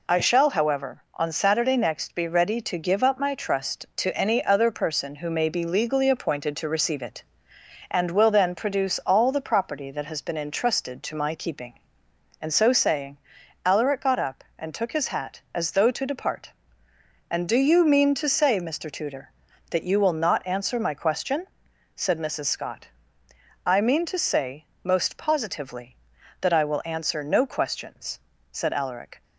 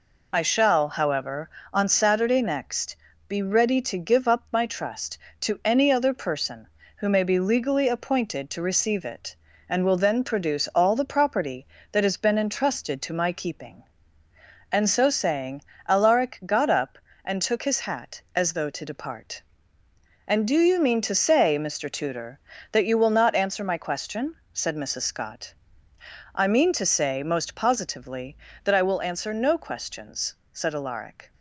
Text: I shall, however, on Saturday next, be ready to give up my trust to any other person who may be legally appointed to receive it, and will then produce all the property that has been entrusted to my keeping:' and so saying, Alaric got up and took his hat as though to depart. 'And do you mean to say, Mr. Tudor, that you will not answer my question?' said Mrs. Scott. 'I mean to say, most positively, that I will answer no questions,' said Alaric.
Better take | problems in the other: neither | none

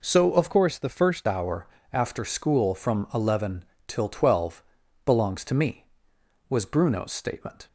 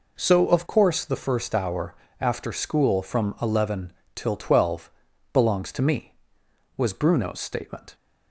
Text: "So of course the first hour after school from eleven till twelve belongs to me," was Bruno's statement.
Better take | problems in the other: second | changes voice from "course" to "first"; from 0.5 to 1.2 s; 0.7 s long // pauses between "hour" and "after"; slight; at 1.6 s; 0.24 s long; slight in the second // pauses between "eleven" and "till"; slight; at 3.6 s; 0.24 s long; slight in the second // pauses between "twelve" and "belongs"; at 4.6 s; 0.42 s long; also in the second

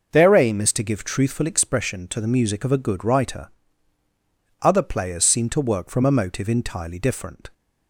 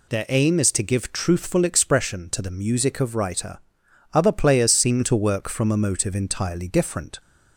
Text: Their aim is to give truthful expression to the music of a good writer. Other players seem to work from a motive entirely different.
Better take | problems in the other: first | skips "a good"; at 3.1 s

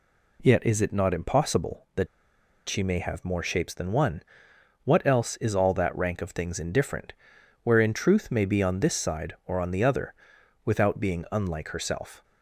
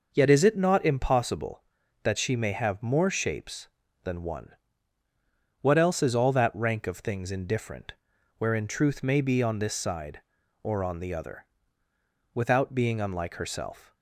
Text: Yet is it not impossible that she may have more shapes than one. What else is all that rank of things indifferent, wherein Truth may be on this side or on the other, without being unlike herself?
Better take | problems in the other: second | pauses between "that" and "she"; noticeable; at 2.0 s; 0.61 s long

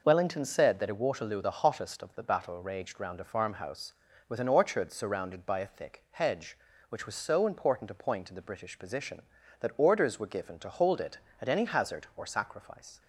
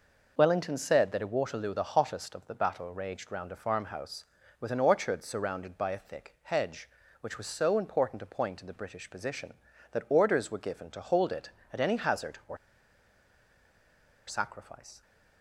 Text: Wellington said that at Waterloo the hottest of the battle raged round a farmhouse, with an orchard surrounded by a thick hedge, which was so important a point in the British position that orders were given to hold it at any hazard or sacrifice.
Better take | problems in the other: first | pauses between "or" and "sacrifice"; strong; at 12.5 s; 1.7 s long

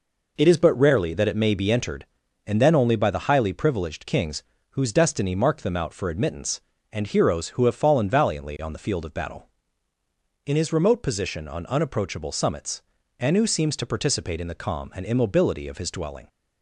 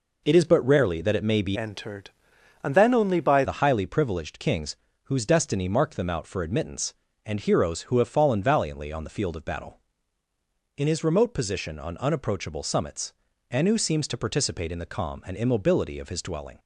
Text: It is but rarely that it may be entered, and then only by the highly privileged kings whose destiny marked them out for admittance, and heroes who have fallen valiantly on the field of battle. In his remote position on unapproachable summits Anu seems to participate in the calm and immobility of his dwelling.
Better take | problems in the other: first | changes voice from "entered" to "by"; from 1.5 to 3.4 s; 1.9 s long // pauses between "kings" and "whose"; slight; at 4.7 s; 0.30 s long; slight in the first // pauses between "summits" and "Anu"; at 13.1 s; 0.38 s long; also in the first

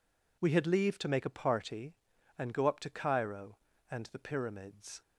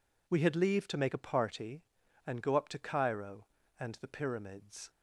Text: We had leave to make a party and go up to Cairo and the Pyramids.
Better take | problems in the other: neither | none

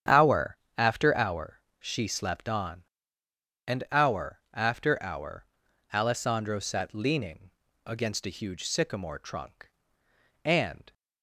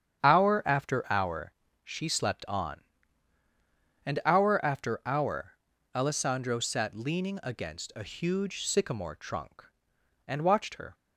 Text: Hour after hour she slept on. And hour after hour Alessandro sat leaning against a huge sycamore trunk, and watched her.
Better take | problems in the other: second | starts louder than the rest; strong; until 1.3 s; 9 dB; strong in the second // pauses between "Hour" and "after"; slight; at 0.5 s; 0.22 s long // pauses between "hour" and "she"; slight; at 1.5 s; 0.22 s long; slight in the second // pauses between "hour" and "Alessandro"; noticeable; at 5.4 s; 0.48 s long; also in the second // pauses between "leaning" and "against"; slight; at 7.5 s; 0.34 s long // stops before "watched her"; at 10.9 s

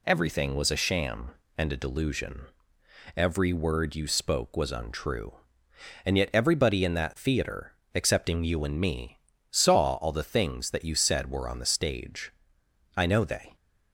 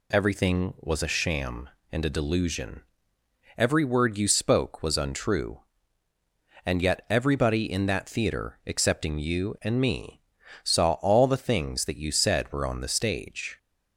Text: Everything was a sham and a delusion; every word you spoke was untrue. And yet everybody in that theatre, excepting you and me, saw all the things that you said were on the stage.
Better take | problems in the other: second | goes on to say "I know they"; from 12.9 s on; 0.60 s long

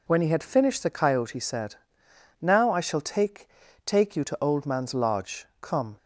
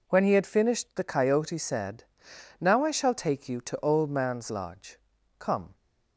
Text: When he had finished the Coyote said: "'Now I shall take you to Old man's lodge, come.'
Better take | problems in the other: second | says "take" twice; at 3.8 s

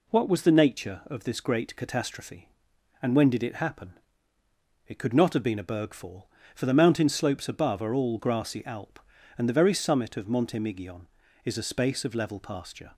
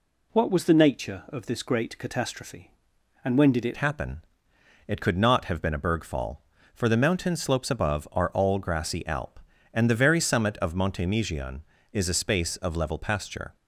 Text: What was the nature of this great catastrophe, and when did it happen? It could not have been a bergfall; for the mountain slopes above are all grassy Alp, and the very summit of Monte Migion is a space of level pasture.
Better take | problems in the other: first | changes voice at "happen"; from 3.7 s on; 9.8 s long

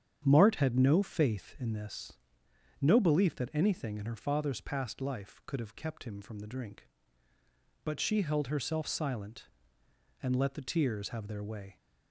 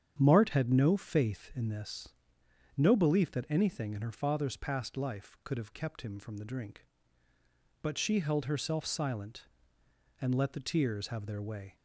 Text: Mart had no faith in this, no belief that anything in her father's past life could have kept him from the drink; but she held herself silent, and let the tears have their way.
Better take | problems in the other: neither | starts louder than the rest; strong; the same in both

